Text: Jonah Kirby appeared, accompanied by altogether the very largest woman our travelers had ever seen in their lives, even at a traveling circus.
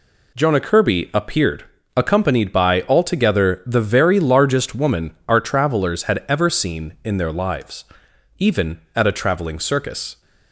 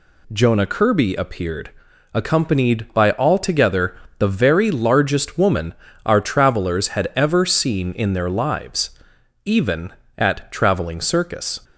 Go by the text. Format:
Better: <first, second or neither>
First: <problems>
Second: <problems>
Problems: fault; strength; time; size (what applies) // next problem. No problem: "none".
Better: first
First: none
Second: pauses between "altogether" and "the"; slight; at 3.9 s; 0.22 s long // pauses between "woman" and "our"; slight; at 5.7 s; 0.30 s long // skips "a"; at 10.5 s